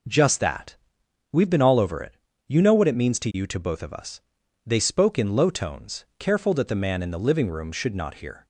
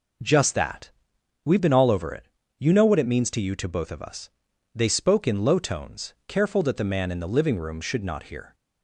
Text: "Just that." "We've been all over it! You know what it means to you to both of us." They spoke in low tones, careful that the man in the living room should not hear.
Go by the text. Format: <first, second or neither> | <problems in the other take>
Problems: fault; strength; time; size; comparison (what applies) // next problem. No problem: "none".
neither | none